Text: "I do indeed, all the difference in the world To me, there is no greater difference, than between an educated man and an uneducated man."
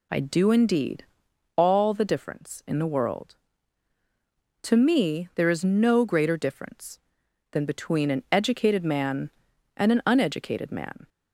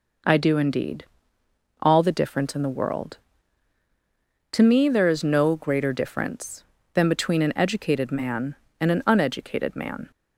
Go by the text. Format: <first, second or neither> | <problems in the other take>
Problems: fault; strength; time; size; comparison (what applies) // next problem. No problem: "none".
neither | none